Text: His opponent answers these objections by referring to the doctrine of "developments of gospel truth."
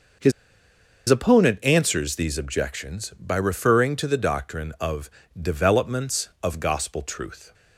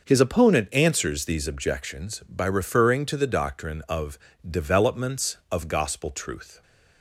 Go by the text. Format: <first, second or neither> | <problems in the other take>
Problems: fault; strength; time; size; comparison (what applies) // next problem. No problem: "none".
second | pauses between "His" and "opponent"; noticeable; at 0.3 s; 0.77 s long // pauses between "of" and "developments"; slight; at 5.0 s; 0.32 s long; slight in the second